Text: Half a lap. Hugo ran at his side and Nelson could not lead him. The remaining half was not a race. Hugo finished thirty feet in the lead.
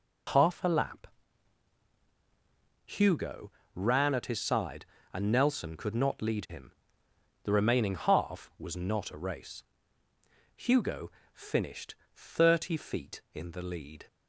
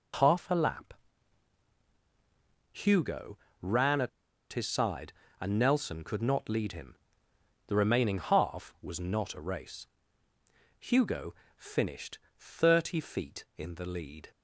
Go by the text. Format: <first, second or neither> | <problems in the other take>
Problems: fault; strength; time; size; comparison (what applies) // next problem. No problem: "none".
first | pauses between "Hugo" and "ran"; slight; at 3.3 s; 0.24 s long; slight in the first // pauses between "at" and "his"; at 4.0 s; 0.43 s long // pauses between "Hugo" and "finished"; slight; at 11.3 s; 0.24 s long; slight in the first // pauses between "finished" and "thirty"; slight; at 12.1 s; 0.18 s long; slight in the first